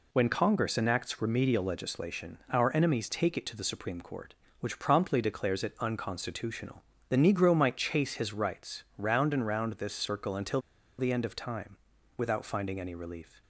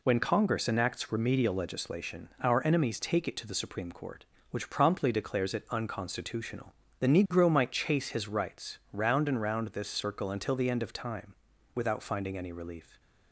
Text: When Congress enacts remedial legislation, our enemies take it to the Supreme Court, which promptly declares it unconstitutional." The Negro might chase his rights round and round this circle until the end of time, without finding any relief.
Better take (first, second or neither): second